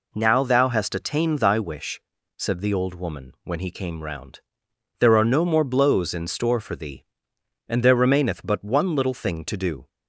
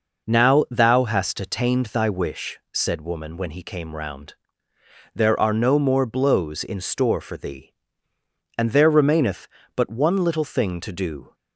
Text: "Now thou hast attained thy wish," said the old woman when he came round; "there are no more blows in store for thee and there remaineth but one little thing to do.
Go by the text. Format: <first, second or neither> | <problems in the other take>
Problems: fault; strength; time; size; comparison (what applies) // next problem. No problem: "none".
first | skips "the old"; at 3.0 s